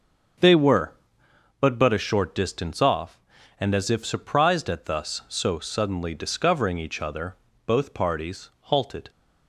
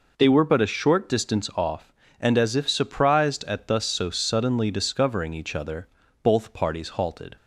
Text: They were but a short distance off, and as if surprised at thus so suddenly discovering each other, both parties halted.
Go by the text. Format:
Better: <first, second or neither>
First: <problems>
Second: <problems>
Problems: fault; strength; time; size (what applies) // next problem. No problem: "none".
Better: second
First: starts louder than the rest; until 2.0 s; 7 dB // says "but" twice; at 1.7 s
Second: none